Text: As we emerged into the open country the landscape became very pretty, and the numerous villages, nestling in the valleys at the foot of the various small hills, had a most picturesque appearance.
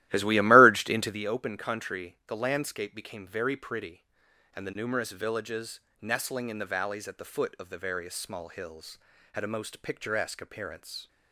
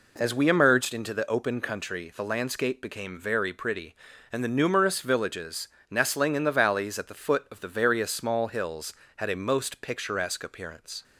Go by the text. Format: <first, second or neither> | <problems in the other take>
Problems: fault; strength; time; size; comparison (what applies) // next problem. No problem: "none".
second | starts louder than the rest; strong; until 1.2 s; 15 dB